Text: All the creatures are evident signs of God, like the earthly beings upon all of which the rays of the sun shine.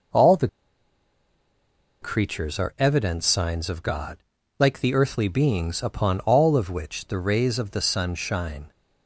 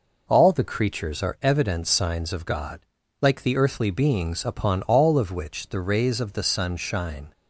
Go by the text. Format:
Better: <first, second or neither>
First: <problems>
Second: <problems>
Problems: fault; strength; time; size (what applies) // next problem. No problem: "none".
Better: second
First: pauses between "the" and "creatures"; strong; at 0.4 s; 1.5 s long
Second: none